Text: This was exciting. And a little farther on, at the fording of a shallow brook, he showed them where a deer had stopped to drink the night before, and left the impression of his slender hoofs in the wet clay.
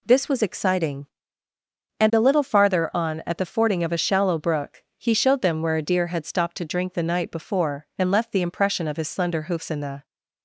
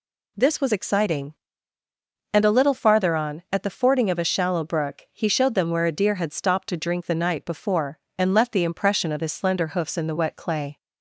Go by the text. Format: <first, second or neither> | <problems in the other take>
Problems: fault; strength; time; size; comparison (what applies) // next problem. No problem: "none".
second | stops before "wet clay"; at 10.0 s